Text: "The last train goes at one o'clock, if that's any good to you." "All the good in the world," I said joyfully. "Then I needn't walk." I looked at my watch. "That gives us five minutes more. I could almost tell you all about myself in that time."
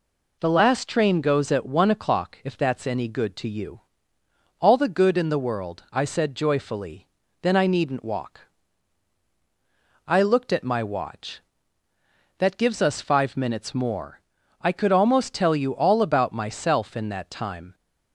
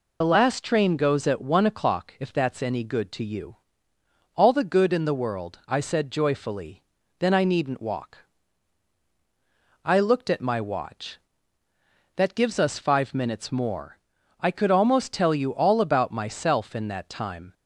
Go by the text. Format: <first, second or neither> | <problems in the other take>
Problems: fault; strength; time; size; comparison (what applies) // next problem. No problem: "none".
first | loses the start of "The"; at 0.2 s; 50 ms